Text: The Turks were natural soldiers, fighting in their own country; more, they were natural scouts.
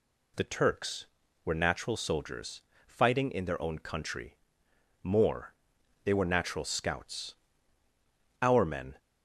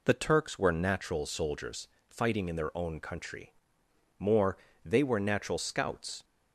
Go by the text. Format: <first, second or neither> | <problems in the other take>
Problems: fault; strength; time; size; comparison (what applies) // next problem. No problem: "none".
second | goes on to say "Our men"; from 8.4 s on; 0.56 s long